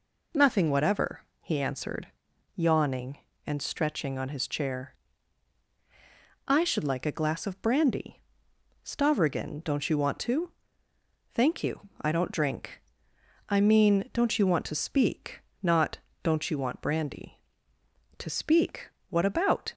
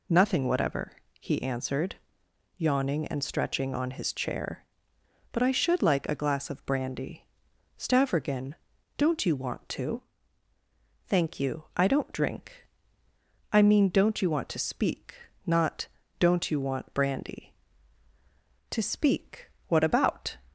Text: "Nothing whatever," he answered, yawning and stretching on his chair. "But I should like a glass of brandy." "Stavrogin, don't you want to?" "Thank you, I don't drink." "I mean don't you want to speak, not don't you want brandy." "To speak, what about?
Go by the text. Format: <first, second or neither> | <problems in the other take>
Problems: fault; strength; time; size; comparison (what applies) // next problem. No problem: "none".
second | skips "But"; at 5.7 s // pauses between "not" and "don't"; slight; at 15.9 s; 0.24 s long; slight in the second